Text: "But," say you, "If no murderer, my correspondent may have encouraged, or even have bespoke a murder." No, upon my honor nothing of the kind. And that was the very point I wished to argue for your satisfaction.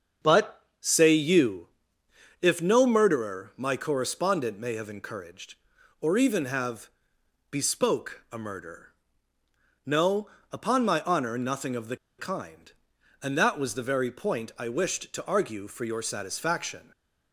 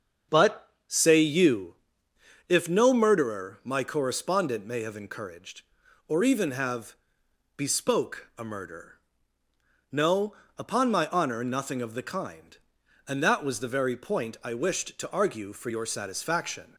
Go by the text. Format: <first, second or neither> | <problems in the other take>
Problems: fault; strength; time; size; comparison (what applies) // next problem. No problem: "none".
second | starts louder than the rest; until 1.3 s; 6.5 dB; also in the second // pauses between "have" and "bespoke"; noticeable; at 6.8 s; 0.64 s long; noticeable in the second // pauses between "the" and "kind"; slight; at 11.9 s; 0.21 s long